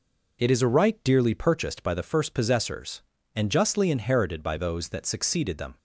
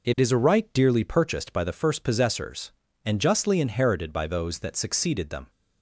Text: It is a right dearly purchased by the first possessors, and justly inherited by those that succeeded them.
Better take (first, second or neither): neither